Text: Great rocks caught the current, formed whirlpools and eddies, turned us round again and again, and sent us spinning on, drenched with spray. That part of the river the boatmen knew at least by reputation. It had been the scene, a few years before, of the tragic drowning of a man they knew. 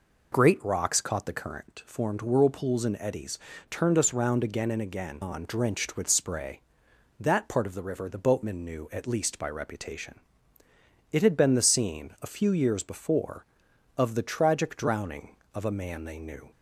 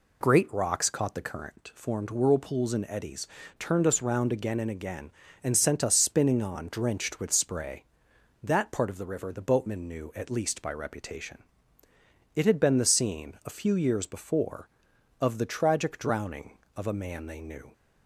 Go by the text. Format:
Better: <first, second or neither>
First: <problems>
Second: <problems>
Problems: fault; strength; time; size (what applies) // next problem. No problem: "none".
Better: second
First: skips "and sent us spinning"; at 5.2 s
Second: none